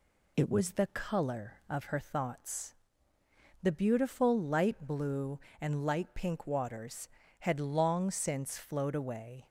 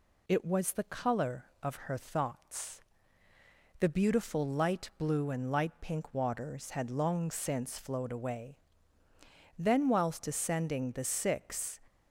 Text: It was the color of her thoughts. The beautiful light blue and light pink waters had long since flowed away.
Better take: first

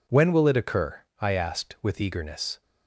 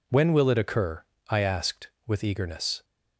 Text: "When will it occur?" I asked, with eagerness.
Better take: neither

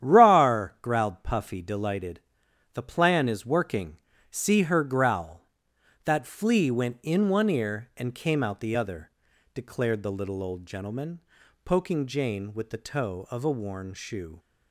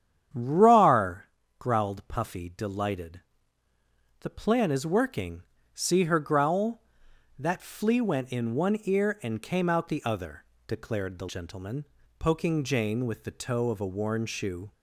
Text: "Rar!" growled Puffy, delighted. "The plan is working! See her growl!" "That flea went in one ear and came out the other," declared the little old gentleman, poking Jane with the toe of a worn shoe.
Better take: first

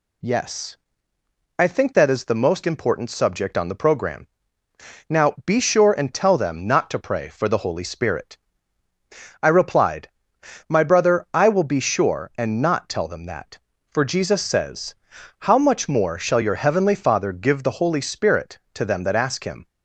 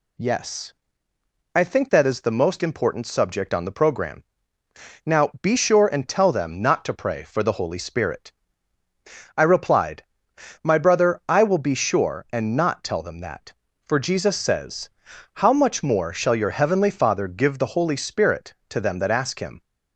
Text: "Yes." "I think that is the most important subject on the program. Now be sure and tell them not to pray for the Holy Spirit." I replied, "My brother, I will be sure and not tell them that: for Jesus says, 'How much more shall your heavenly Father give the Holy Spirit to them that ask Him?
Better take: neither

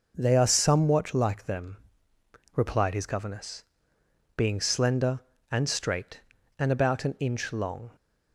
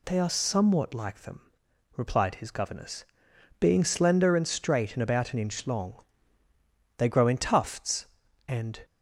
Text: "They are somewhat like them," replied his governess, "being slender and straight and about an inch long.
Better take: first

